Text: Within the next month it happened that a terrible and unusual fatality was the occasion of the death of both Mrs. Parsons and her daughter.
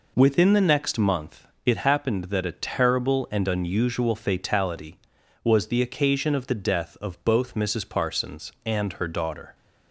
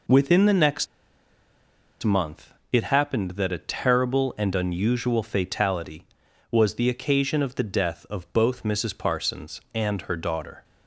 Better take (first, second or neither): first